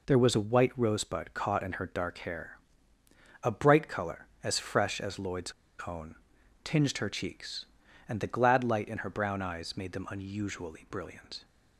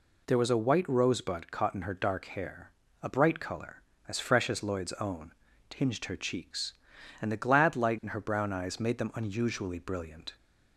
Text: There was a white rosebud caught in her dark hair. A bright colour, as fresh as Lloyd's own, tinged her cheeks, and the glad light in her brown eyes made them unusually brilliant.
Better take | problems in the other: second | pauses between "Lloyd's" and "own"; slight; at 5.5 s; 0.33 s long

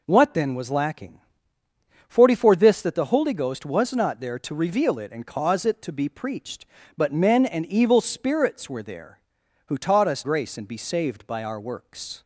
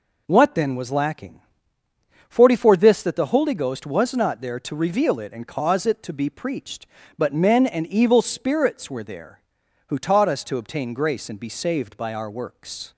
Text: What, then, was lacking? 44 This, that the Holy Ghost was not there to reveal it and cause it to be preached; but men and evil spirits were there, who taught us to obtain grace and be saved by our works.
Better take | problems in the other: second | skips "to obtain"; at 10.2 s

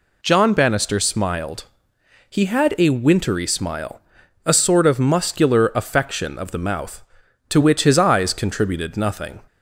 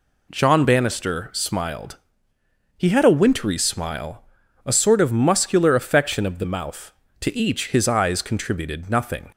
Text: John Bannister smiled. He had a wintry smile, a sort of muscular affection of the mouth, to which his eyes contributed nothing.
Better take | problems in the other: first | says "each" for "which"; at 7.3 s

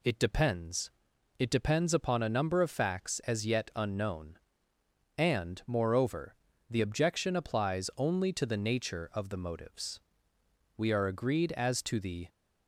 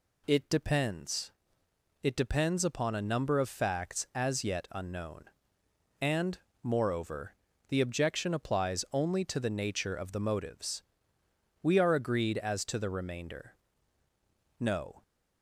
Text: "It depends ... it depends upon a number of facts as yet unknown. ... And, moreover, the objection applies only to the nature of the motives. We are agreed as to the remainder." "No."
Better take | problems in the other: second | stops before "remainder No"; at 12.2 s

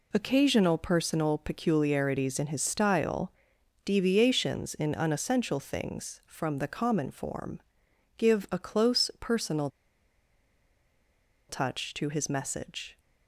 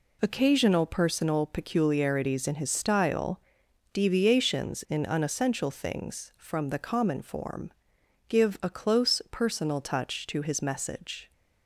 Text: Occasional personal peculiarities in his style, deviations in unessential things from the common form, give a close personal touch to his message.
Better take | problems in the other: second | pauses between "personal" and "touch"; strong; at 9.6 s; 1.8 s long

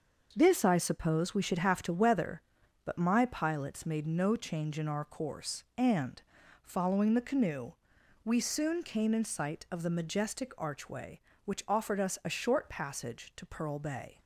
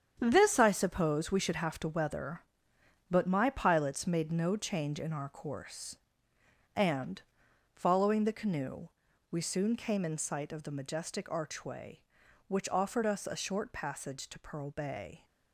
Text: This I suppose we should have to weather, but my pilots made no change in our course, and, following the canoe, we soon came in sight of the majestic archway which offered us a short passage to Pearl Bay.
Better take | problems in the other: first | gets quieter; strong; throughout; 9.5 dB

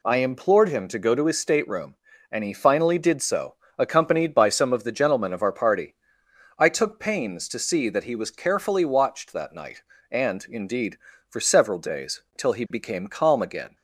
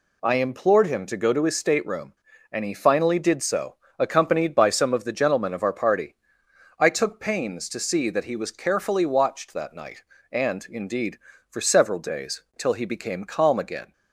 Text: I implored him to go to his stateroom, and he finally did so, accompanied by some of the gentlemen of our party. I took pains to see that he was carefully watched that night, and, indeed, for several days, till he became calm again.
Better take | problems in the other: neither | none

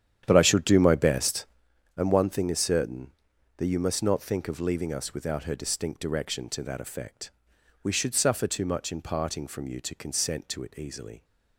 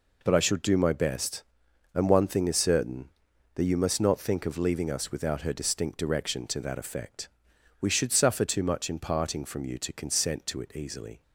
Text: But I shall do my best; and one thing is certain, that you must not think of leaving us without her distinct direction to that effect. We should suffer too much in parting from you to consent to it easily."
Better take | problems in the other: second | starts louder than the rest; strong; until 1.7 s; 9.5 dB

